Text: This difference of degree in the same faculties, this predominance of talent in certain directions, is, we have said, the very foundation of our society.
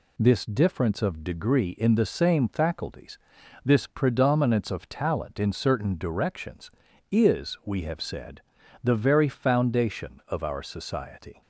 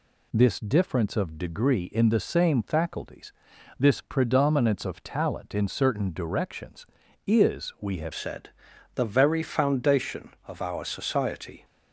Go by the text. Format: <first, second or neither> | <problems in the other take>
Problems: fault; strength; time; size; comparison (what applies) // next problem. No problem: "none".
first | changes voice at "said"; from 8.1 s on; 3.5 s long